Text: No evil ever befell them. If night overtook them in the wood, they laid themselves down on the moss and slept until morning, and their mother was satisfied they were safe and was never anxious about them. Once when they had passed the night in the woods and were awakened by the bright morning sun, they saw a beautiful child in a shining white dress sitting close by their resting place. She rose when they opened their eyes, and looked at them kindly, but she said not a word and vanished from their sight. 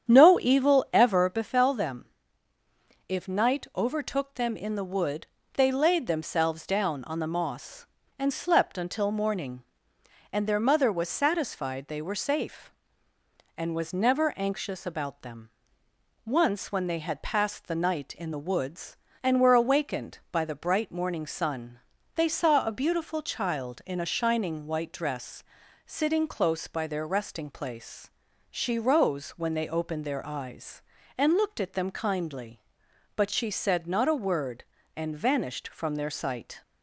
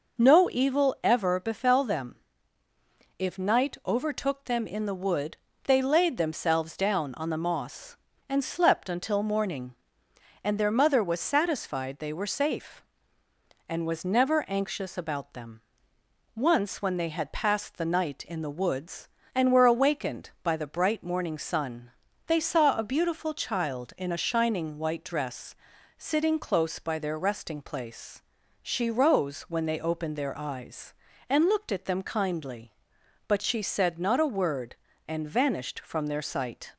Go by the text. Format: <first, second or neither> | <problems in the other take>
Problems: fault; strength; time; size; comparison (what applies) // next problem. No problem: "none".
second | starts louder than the rest; strong; until 1.5 s; 8.5 dB // pauses between "dress" and "sitting"; at 25.4 s; 0.42 s long; also in the second